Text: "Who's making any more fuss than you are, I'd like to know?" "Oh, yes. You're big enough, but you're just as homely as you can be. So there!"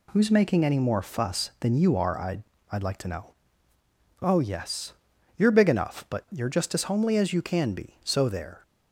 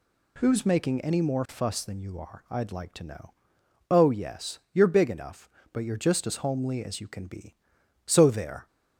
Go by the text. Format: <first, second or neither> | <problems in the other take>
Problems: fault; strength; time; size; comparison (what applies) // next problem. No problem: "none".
second | says "I'd" twice; at 2.7 s